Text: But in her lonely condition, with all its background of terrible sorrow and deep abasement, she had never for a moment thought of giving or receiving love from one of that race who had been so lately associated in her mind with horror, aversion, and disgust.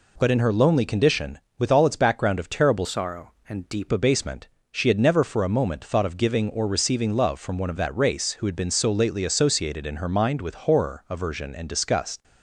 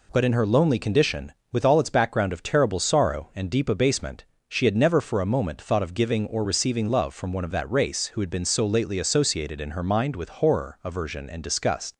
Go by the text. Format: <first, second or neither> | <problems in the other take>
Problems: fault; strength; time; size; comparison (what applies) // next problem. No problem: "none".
second | changes voice from "sorrow" to "deep"; from 2.8 to 3.8 s; 1.0 s long